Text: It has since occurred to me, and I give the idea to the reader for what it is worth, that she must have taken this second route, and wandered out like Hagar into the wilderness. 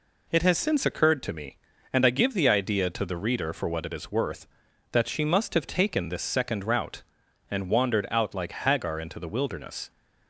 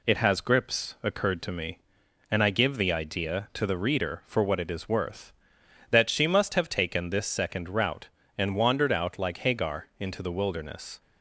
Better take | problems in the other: first | says "grips" for "since"; at 0.4 s

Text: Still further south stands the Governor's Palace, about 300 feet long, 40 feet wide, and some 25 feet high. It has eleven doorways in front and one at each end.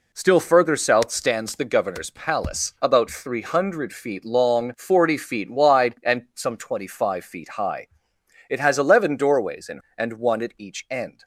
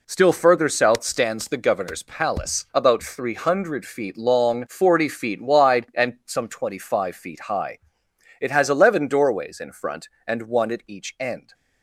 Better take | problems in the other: second | skips "front"; at 9.8 s

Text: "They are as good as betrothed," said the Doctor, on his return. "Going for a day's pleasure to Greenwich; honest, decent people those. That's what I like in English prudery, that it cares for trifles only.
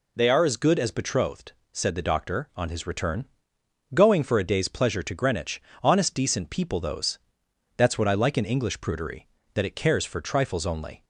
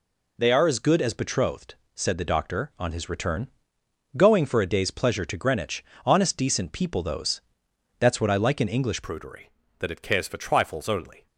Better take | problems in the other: first | changes voice at "prudery"; from 9.0 s on; 2.2 s long

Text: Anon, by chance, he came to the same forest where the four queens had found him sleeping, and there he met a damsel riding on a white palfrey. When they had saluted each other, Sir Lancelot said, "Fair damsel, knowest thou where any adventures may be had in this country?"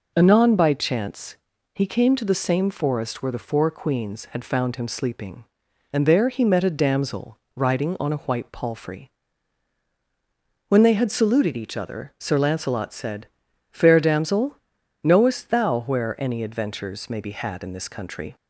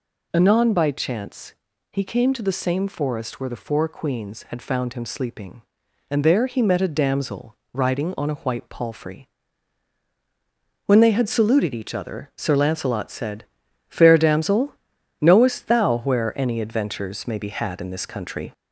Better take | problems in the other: first | gets louder; slight; throughout; 3 dB // pauses between "damsel" and "riding"; slight; at 7.5 s; 0.16 s long; slight in the first

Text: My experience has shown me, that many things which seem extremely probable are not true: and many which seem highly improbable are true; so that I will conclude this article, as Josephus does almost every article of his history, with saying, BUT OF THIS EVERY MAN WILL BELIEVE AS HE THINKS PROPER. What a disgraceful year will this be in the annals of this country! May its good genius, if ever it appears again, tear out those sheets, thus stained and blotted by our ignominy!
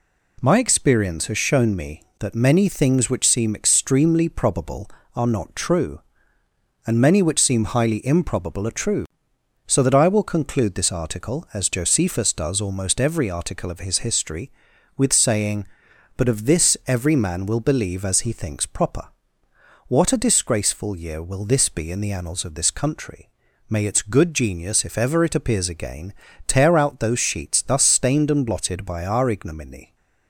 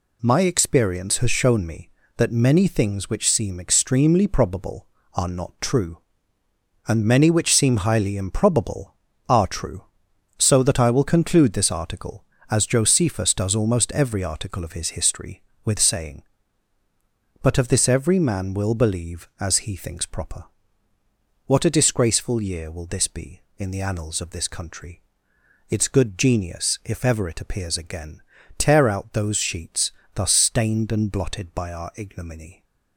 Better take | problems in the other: first | skips "May"; at 25.3 s

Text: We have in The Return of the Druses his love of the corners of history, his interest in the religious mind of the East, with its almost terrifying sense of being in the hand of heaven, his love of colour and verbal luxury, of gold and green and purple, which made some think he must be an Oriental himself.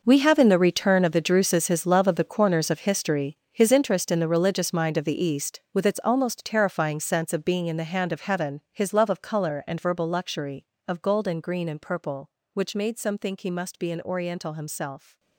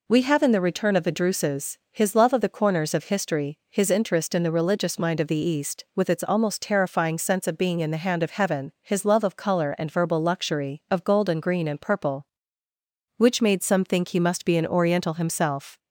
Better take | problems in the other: second | gets quieter; strong; throughout; 15 dB

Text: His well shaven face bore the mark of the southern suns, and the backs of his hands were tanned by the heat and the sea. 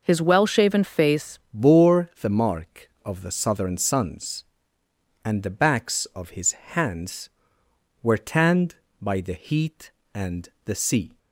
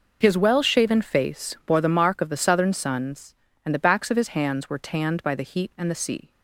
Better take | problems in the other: second | changes voice at "bore"; from 1.5 s on; 9.6 s long // pauses between "and" and "the"; slight; at 10.4 s; 0.16 s long

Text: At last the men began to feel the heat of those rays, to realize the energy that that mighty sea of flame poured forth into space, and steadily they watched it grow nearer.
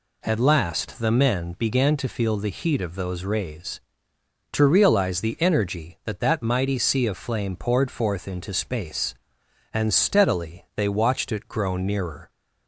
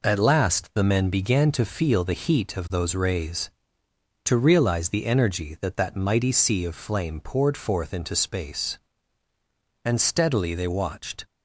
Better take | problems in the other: first | stops before "it grow nearer"; at 11.2 s

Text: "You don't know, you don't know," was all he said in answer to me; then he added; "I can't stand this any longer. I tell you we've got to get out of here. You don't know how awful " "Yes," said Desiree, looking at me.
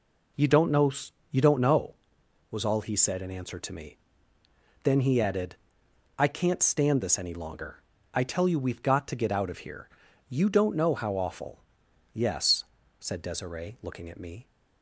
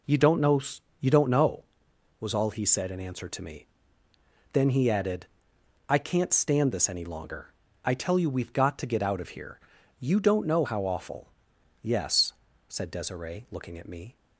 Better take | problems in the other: neither | none

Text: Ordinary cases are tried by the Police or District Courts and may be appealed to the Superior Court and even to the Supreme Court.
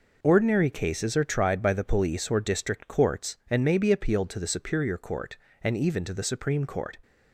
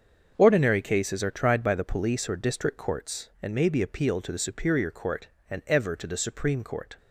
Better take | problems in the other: first | starts louder than the rest; until 1.3 s; 6.5 dB // says "ever" for "even"; at 5.6 s

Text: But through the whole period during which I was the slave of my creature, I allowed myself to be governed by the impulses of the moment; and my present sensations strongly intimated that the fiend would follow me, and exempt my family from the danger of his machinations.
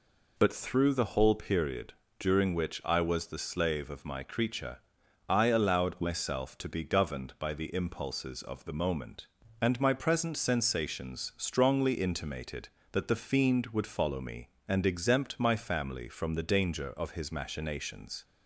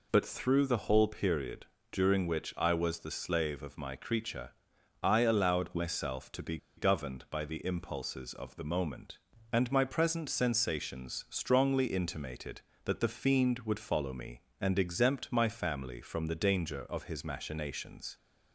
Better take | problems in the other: first | pauses between "period" and "during"; slight; at 1.6 s; 0.24 s long; slight in the first // pauses between "be" and "governed"; slight; at 6.5 s; 0.20 s long

